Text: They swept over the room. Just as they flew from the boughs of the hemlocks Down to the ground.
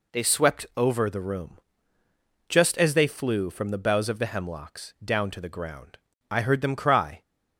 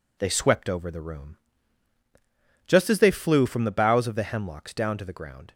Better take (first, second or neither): second